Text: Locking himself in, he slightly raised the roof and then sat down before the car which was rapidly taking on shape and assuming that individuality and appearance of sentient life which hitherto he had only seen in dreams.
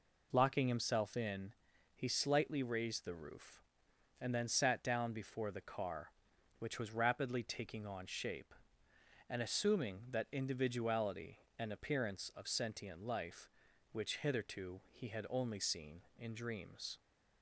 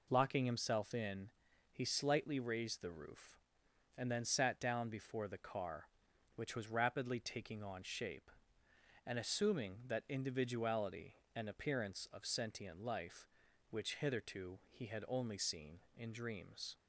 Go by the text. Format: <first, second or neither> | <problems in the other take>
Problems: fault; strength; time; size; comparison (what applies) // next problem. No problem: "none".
neither | none